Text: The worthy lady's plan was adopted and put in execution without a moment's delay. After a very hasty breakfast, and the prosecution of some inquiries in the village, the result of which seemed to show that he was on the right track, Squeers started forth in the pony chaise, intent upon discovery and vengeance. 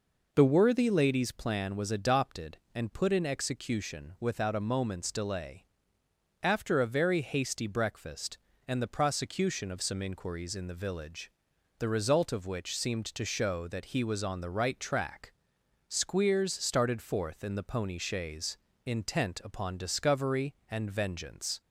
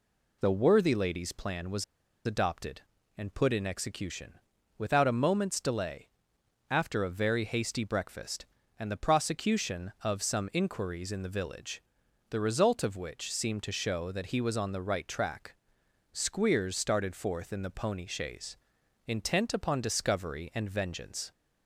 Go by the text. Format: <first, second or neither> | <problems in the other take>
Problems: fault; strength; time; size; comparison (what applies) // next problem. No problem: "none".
first | pauses between "was" and "adopted"; at 1.8 s; 0.43 s long // pauses between "execution" and "without"; at 4.3 s; 0.42 s long